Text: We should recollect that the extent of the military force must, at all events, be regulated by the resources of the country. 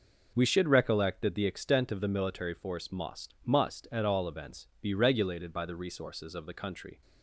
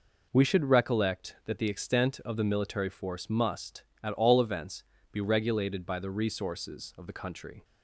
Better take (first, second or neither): second